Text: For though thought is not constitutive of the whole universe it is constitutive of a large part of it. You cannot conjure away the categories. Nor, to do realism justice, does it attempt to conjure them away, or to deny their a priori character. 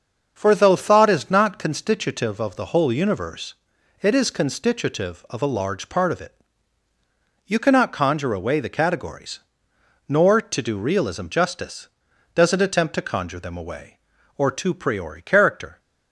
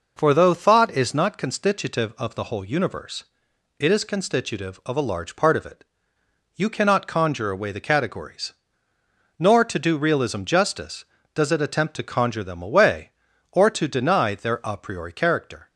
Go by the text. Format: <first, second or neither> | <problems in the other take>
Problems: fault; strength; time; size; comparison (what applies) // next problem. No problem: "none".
second | starts louder than the rest; until 1.3 s; 6.5 dB // pauses between "universe" and "it"; noticeable; at 3.5 s; 0.48 s long; noticeable in the second // skips "deny their a"; at 14.7 s